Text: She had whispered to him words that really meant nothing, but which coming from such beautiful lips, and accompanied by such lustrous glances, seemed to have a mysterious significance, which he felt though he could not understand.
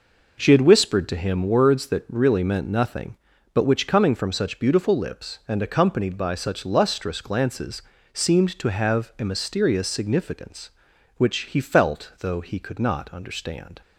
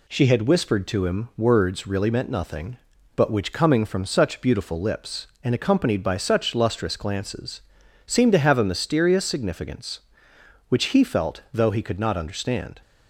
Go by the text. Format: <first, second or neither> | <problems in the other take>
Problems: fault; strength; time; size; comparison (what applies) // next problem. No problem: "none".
first | skips "that"; at 1.8 s